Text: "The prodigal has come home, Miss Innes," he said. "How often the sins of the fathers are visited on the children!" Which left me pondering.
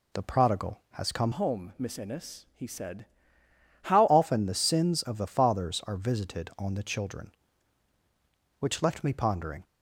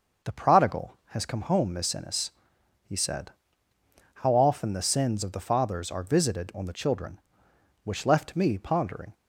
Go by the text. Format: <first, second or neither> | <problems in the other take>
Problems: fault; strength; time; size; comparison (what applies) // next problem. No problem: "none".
second | changes voice from "home" to "How"; from 1.3 to 4.0 s; 2.7 s long